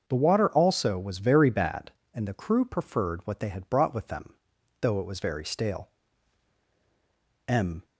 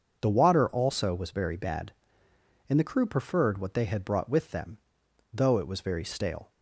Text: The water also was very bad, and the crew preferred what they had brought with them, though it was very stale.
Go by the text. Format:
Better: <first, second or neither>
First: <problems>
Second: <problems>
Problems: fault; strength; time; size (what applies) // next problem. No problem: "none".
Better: second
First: starts louder than the rest; until 1.0 s; 6.5 dB // goes on to say "M"; slight; from 7.4 s on; 0.38 s long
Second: none